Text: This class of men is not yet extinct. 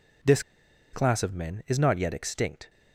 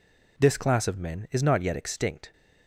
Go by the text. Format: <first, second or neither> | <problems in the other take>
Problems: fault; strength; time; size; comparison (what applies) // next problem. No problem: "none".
second | pauses between "This" and "class"; noticeable; at 0.4 s; 0.51 s long